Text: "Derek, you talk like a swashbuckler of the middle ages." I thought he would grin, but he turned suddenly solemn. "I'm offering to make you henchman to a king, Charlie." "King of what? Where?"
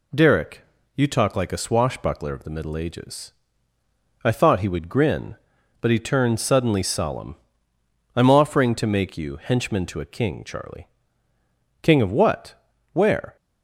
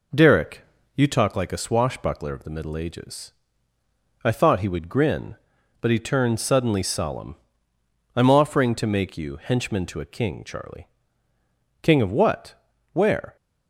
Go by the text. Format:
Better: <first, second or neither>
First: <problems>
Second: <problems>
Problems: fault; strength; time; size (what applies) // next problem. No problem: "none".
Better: first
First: none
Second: starts louder than the rest; noticeable; until 1.3 s; 4 dB